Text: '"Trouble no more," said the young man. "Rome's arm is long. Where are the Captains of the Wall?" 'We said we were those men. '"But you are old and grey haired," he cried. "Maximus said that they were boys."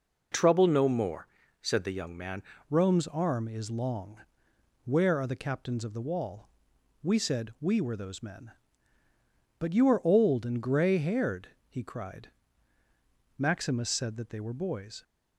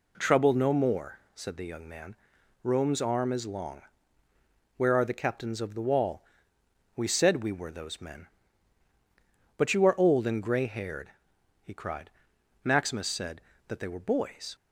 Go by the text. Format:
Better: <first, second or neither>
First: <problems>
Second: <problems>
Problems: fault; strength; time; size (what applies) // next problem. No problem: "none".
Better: second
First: changes voice at "Rome's"; from 2.6 s on; 12.4 s long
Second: none